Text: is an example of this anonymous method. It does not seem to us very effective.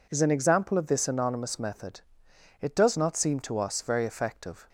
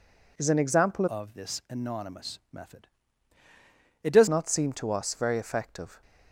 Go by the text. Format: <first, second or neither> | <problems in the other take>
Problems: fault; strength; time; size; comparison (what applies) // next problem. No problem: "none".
first | changes voice from "of" to "does"; from 1.0 to 4.2 s; 3.2 s long